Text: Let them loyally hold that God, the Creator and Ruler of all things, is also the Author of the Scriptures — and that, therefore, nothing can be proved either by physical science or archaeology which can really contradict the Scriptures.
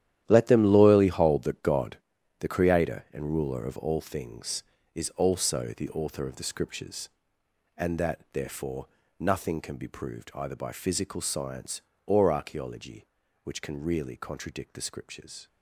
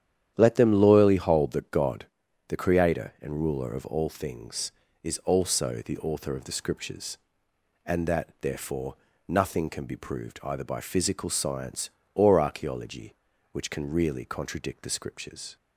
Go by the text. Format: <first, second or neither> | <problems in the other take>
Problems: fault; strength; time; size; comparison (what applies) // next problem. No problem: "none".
second | gets quieter; strong; throughout; 12.5 dB // starts louder than the rest; strong; until 1.2 s; 11.5 dB; strong in the second